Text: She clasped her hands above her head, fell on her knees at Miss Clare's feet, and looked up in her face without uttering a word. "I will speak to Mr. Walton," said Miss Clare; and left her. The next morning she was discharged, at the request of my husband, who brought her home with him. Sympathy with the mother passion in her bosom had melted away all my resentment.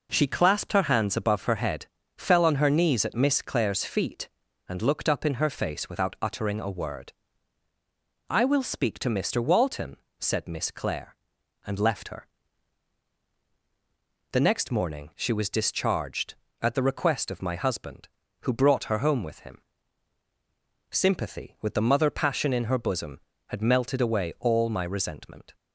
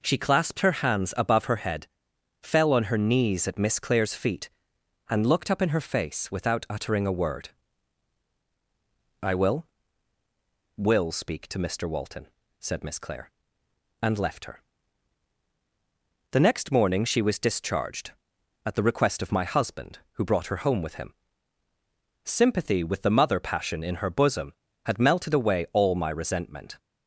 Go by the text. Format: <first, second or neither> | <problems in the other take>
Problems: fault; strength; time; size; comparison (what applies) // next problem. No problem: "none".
first | says "will" twice; at 10.7 s